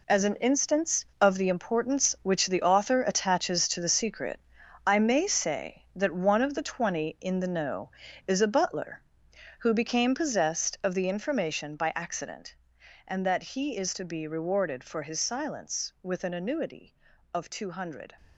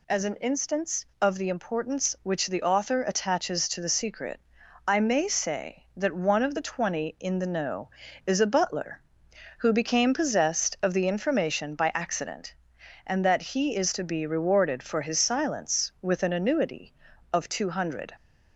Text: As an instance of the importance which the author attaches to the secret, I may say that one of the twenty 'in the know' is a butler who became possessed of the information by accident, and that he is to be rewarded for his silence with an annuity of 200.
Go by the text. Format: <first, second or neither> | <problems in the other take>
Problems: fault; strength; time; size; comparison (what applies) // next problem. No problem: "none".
second | gets quieter; strong; throughout; 10 dB